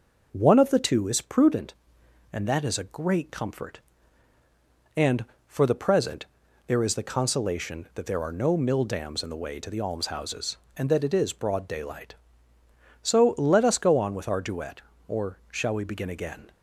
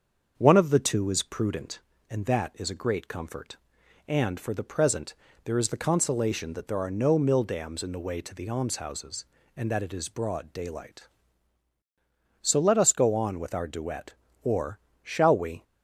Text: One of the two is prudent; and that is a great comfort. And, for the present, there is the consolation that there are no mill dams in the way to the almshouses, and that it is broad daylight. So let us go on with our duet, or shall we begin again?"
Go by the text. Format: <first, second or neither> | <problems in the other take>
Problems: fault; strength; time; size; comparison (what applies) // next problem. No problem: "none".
first | starts louder than the rest; until 1.4 s; 7 dB // pauses between "or" and "shall"; slight; at 14.7 s; 0.24 s long // stops before "begin again"; at 15.6 s